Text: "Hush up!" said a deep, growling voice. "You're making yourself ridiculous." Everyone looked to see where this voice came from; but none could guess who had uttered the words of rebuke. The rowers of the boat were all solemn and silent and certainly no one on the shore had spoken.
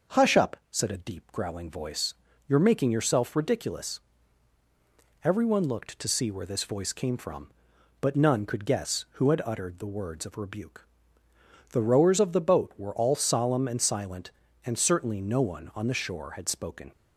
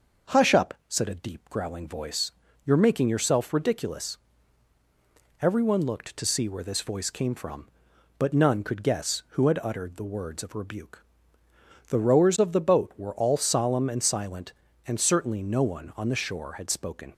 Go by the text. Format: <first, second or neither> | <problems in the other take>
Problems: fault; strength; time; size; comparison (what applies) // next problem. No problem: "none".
neither | starts louder than the rest; noticeable; the same in both